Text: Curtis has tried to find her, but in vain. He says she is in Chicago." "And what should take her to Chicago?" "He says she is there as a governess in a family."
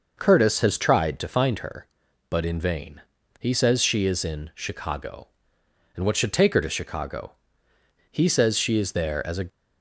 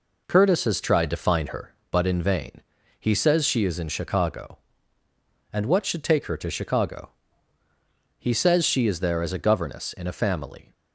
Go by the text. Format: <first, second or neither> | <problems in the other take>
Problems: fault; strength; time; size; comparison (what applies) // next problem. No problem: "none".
second | stops before "governess in a family"; at 9.4 s